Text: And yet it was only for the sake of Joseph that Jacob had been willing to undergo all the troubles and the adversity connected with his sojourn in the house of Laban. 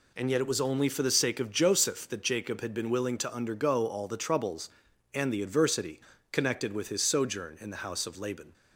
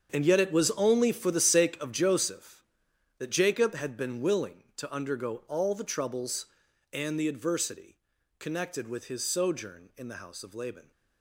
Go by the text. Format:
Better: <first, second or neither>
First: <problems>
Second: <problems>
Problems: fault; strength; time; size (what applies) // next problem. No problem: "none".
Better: first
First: pauses between "adversity" and "connected"; slight; at 6.0 s; 0.30 s long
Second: gets quieter; strong; throughout; 13.5 dB // pauses between "adversity" and "connected"; at 7.9 s; 0.42 s long